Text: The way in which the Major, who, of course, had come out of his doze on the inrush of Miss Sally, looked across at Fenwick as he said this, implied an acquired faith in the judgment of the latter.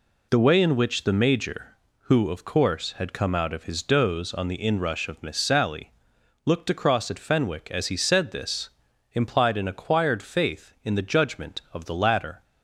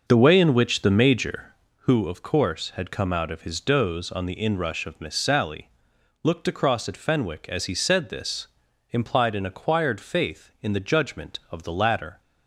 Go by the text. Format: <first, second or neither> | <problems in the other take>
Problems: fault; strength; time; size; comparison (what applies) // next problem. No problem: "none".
first | starts louder than the rest; noticeable; until 1.9 s; 6 dB